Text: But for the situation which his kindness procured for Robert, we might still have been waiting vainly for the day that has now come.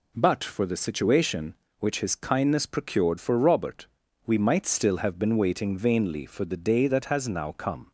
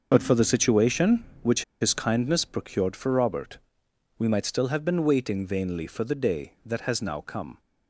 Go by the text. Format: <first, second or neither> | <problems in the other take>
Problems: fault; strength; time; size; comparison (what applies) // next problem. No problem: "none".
first | starts louder than the rest; noticeable; until 1.1 s; 6 dB // pauses between "which" and "his"; slight; at 1.6 s; 0.18 s long